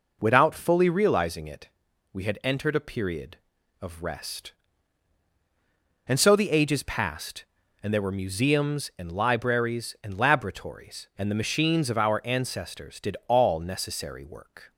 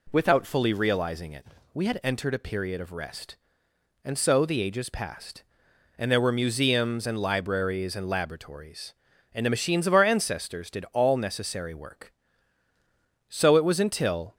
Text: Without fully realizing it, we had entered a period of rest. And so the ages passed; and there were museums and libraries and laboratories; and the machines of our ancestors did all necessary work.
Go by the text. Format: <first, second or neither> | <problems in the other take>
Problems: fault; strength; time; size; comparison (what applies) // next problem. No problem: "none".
first | goes on to say "So it was until"; noticeable; from 13.2 s on; 1.0 s long